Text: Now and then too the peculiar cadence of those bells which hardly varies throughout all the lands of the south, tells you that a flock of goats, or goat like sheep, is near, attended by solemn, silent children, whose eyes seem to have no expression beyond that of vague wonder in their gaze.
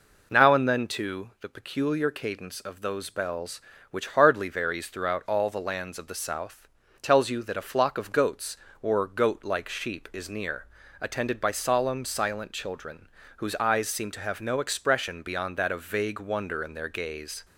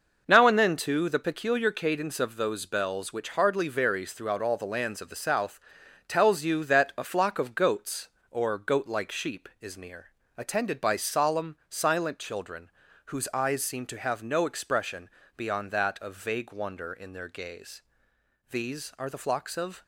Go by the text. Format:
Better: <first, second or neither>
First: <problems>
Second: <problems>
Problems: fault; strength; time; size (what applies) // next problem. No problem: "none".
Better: first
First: none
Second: pauses between "expression" and "beyond"; slight; at 15.0 s; 0.28 s long // goes on to say "These are the flocks of"; from 18.5 s on; 1.3 s long